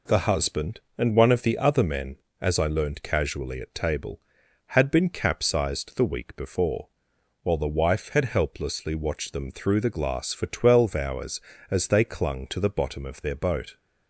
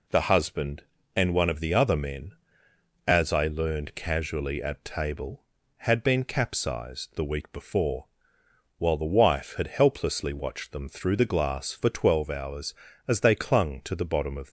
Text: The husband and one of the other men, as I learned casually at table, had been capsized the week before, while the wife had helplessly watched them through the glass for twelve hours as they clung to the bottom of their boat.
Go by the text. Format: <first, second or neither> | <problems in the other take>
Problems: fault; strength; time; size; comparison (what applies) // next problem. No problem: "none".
first | stops before "their boat"; at 14.4 s